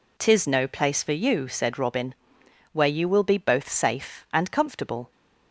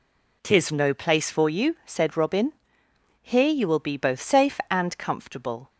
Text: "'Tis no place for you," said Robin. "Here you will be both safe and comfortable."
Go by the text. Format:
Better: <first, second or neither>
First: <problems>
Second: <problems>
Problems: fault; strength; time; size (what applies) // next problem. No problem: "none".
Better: second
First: says "Where" for "Here"; at 2.7 s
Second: none